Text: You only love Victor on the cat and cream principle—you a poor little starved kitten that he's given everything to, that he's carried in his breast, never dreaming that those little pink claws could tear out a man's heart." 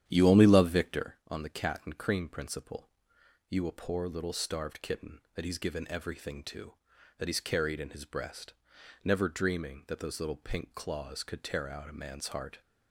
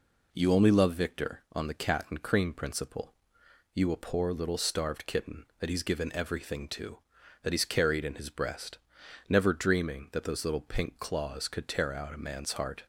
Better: second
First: starts louder than the rest; strong; until 1.1 s; 10 dB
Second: none

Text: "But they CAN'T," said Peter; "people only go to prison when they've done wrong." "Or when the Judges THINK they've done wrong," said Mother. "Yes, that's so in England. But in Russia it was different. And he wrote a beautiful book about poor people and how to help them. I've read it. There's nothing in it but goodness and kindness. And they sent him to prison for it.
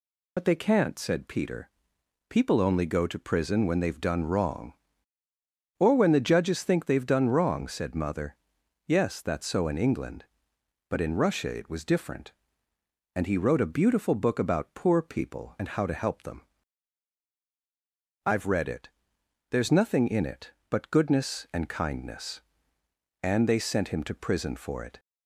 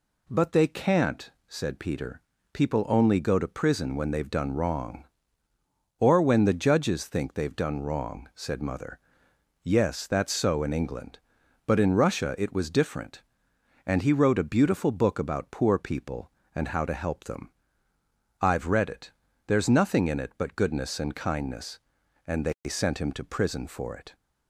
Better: second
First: loses the start of "But"; at 0.3 s; 55 ms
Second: none

